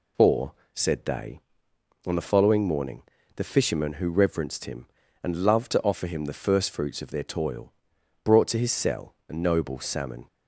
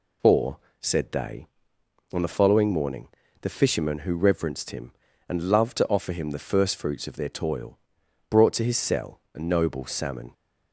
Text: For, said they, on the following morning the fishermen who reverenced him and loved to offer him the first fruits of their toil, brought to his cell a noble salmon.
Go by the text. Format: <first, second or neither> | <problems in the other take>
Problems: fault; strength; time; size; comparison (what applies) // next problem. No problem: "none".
neither | pauses between "morning" and "the"; slight; the same in both